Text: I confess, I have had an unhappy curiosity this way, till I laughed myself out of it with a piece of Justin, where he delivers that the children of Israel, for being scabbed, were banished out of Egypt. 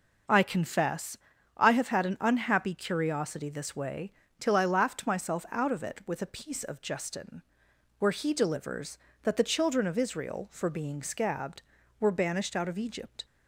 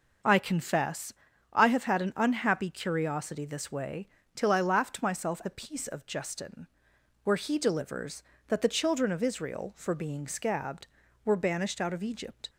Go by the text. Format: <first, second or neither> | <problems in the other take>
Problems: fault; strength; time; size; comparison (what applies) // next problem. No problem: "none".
first | skips "out of it with"; at 5.4 s